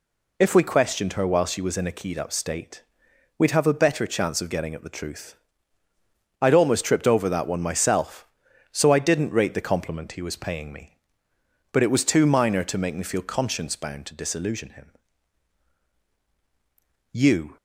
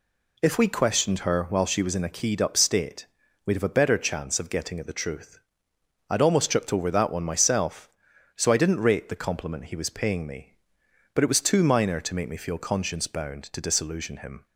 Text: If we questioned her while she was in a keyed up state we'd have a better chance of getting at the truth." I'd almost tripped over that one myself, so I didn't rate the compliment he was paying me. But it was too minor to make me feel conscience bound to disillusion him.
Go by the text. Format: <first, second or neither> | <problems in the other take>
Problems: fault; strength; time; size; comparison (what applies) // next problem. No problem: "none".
second | pauses between "state" and "we'd"; noticeable; at 2.8 s; 0.54 s long; slight in the second // goes on to say "You"; slight; from 17.1 s on; 0.44 s long